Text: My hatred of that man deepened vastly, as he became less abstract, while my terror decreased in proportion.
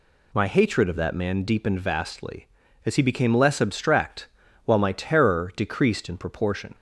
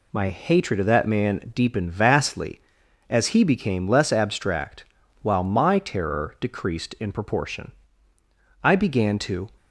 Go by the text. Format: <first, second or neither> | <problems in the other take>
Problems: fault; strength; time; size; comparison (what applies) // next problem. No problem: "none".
first | goes on to say "I began to"; noticeable; from 8.6 s on; 0.86 s long